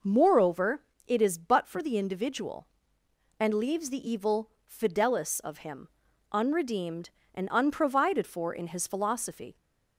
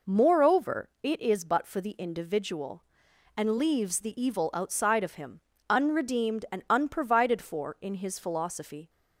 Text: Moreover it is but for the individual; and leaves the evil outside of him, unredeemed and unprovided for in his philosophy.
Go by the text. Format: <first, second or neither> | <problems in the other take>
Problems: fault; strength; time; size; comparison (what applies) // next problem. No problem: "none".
second | pauses between "Moreover" and "it"; slight; at 0.8 s; 0.26 s long // says "fidelis" for "outside"; at 4.6 s